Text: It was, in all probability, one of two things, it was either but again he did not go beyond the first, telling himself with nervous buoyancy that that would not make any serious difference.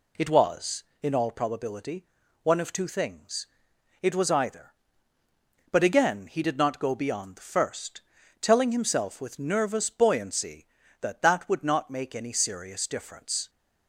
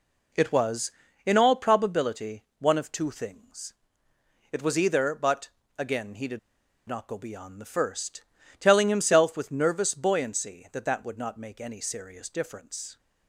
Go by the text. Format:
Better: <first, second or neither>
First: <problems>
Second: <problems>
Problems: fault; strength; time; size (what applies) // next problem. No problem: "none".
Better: first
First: none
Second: pauses between "but" and "again"; slight; at 5.4 s; 0.30 s long // pauses between "did" and "not"; noticeable; at 6.3 s; 0.50 s long